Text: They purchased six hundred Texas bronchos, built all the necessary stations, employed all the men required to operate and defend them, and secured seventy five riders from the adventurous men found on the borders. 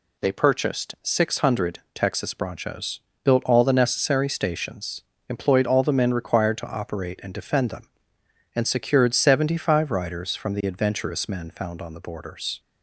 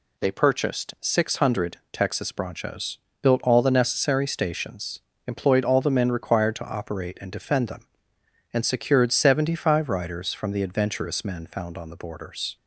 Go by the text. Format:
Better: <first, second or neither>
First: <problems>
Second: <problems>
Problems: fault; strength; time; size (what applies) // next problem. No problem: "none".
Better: neither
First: none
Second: none